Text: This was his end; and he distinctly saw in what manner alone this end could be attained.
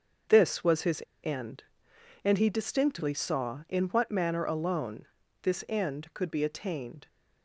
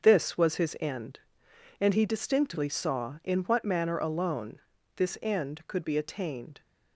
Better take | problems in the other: second | starts louder than the rest; until 1.4 s; 6.5 dB; also in the second // pauses between "his" and "end"; slight; at 1.0 s; 0.19 s long // pauses between "alone" and "this"; at 5.0 s; 0.38 s long; also in the second

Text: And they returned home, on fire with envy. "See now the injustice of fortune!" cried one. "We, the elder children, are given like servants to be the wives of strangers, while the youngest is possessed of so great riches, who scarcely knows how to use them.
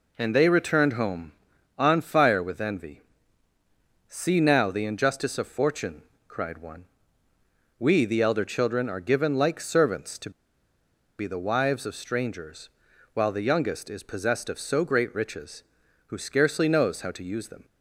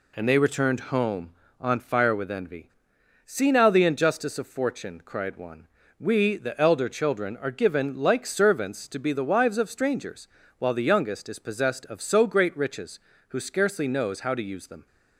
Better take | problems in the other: second | pauses between "to" and "be"; noticeable; at 10.3 s; 0.88 s long

